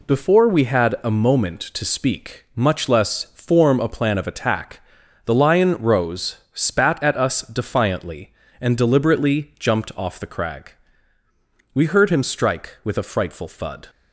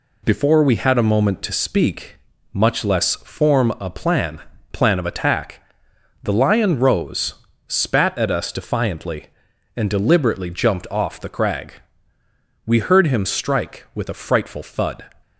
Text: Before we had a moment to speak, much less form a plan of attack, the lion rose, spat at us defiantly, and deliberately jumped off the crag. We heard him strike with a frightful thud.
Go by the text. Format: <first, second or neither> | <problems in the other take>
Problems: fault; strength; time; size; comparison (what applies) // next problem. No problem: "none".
first | says "plan" twice; at 4.7 s